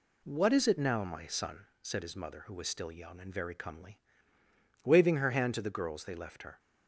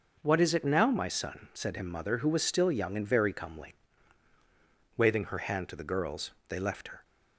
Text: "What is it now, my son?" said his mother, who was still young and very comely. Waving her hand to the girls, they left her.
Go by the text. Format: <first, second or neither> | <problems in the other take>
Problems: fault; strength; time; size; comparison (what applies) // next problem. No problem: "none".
first | says "him" for "his"; at 1.7 s